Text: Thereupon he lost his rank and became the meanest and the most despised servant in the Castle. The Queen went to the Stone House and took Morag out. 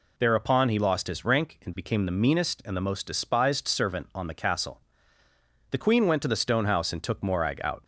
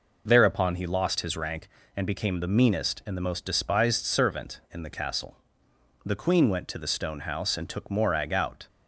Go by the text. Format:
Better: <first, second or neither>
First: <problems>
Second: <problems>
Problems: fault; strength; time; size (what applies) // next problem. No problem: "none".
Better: second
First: says "on" for "in"; at 4.1 s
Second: none